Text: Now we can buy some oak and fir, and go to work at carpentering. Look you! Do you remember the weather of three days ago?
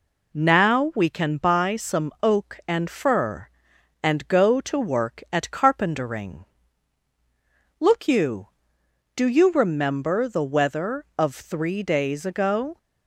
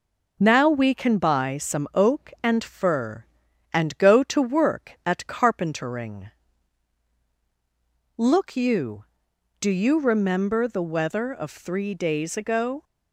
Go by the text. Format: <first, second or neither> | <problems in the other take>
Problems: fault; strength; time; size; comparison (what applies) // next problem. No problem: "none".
neither | none